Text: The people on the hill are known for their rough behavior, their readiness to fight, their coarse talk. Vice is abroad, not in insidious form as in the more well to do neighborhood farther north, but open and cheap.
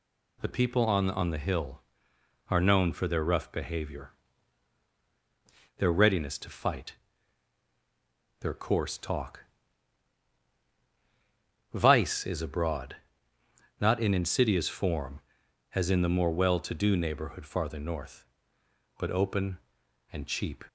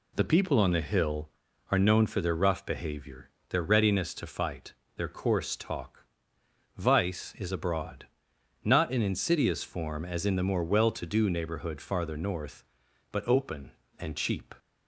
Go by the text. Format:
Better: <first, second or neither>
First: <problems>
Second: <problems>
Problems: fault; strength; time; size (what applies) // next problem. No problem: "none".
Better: second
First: says "on" twice; at 1.1 s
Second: none